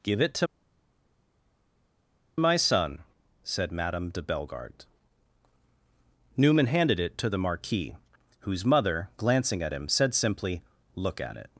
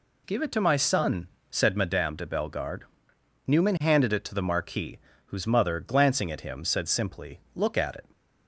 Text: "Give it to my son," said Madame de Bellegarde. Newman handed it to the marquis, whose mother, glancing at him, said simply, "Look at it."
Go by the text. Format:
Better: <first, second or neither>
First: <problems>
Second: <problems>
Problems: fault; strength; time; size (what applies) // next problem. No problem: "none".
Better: second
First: pauses between "to" and "my"; strong; at 0.4 s; 1.9 s long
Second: none